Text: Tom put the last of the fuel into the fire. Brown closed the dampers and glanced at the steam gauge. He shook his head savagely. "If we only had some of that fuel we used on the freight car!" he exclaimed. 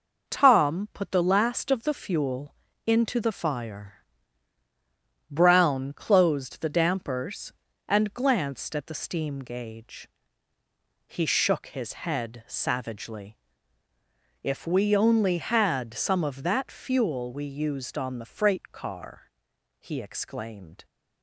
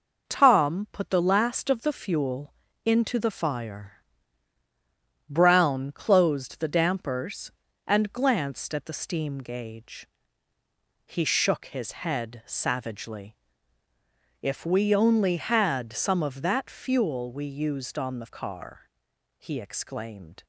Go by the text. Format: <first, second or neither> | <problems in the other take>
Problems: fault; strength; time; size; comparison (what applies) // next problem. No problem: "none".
first | pauses between "fuel" and "into"; slight; at 2.5 s; 0.30 s long; slight in the first // skips "freight"; at 18.2 s